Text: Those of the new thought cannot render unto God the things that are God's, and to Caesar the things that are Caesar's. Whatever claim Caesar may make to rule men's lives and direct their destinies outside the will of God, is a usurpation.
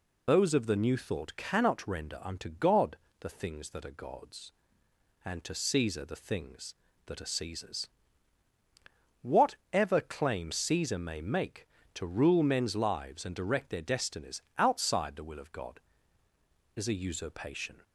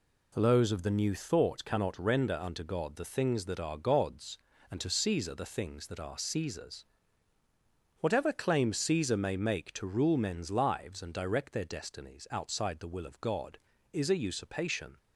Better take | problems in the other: second | loses the start of "Those"; at 0.2 s; 30 ms // pauses between "God" and "the"; slight; at 2.9 s; 0.24 s long // pauses between "destinies" and "outside"; slight; at 14.4 s; 0.16 s long

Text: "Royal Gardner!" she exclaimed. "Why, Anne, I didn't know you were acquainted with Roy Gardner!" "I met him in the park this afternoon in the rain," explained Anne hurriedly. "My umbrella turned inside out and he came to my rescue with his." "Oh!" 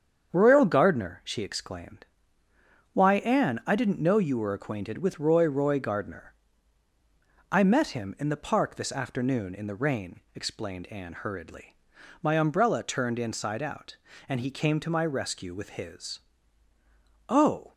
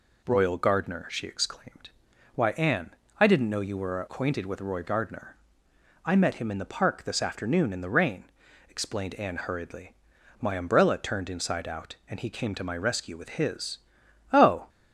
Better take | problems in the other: second | starts louder than the rest; strong; until 1.3 s; 7.5 dB // says "Roy" twice; at 5.4 s

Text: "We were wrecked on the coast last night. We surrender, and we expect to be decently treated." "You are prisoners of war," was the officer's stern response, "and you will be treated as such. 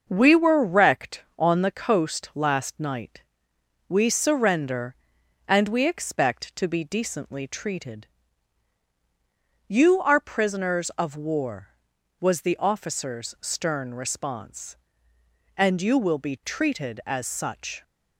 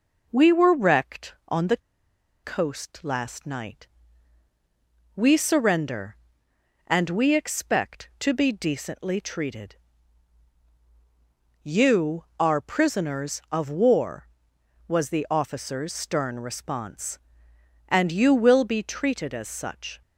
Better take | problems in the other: first | pauses between "the" and "coast"; noticeable; at 1.7 s; 0.67 s long

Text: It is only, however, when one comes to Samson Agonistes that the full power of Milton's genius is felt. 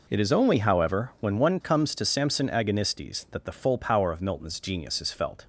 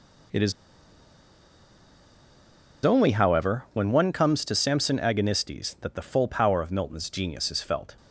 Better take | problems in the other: first | pauses between "is" and "only"; strong; at 0.5 s; 2.3 s long

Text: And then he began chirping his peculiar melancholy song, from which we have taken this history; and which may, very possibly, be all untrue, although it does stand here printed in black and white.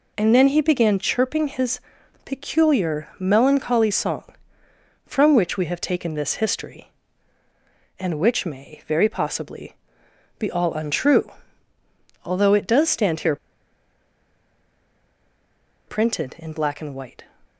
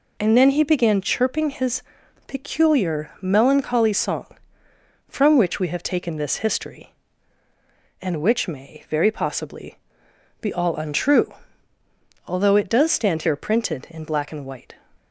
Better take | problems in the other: second | pauses between "his" and "peculiar"; at 1.7 s; 0.44 s long; also in the second // pauses between "here" and "printed"; strong; at 13.3 s; 2.5 s long

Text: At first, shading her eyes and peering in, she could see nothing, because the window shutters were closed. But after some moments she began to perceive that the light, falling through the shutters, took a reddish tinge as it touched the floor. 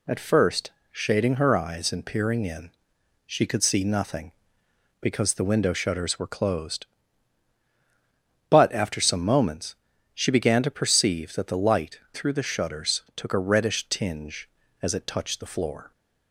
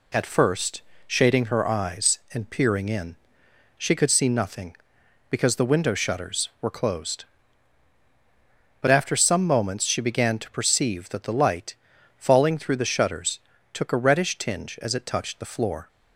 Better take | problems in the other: second | pauses between "moments" and "she"; at 9.7 s; 0.42 s long // skips "falling"; at 12.0 s

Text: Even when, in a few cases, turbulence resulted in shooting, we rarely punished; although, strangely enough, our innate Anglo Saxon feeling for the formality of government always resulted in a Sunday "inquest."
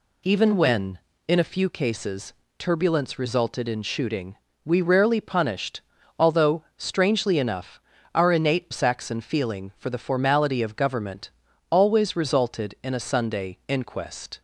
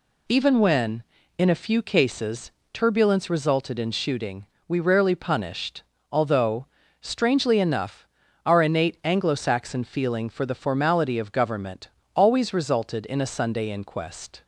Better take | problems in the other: second | skips "Anglo"; at 8.7 s // pauses between "government" and "always"; at 11.2 s; 0.42 s long; slight in the second

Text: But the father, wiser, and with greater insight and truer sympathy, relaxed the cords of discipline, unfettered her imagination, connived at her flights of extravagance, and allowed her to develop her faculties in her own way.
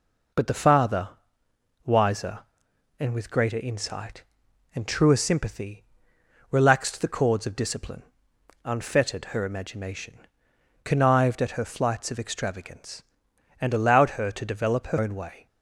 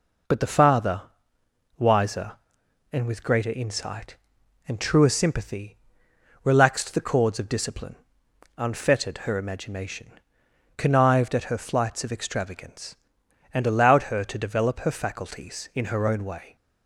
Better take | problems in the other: second | skips "faculties in her"; at 14.9 s

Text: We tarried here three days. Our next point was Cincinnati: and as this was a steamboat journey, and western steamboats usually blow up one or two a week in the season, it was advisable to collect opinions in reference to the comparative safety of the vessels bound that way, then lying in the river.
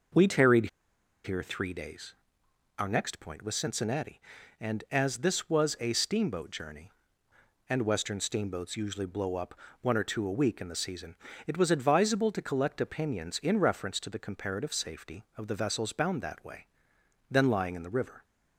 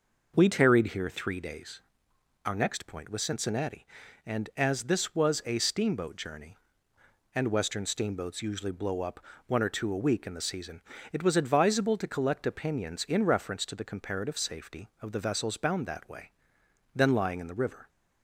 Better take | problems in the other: second | pauses between "tarried" and "here"; noticeable; at 0.6 s; 0.57 s long // pauses between "up" and "one"; slight; at 9.5 s; 0.26 s long; slight in the second

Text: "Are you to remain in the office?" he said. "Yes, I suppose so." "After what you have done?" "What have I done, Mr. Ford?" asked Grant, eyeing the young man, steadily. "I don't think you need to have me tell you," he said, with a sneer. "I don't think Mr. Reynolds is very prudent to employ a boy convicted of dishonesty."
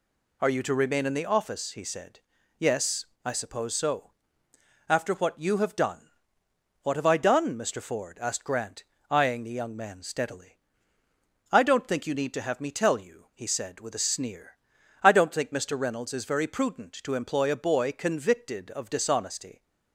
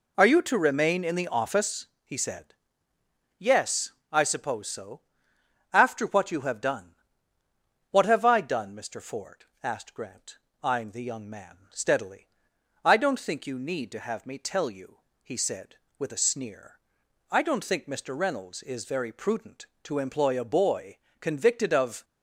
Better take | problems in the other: first | pauses between "boy" and "convicted"; slight; at 20.9 s; 0.22 s long // stops before "dishonesty"; at 22.0 s

